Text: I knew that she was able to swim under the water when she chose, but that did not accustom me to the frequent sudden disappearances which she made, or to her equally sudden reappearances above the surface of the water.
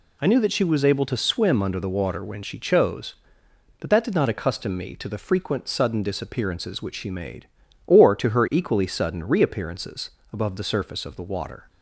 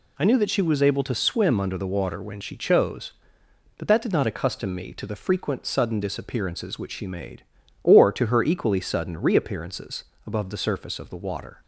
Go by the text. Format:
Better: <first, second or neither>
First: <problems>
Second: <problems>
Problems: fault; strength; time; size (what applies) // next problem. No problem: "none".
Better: neither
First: pauses between "reappearances" and "above"; slight; at 10.0 s; 0.24 s long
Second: pauses between "reappearances" and "above"; slight; at 10.0 s; 0.24 s long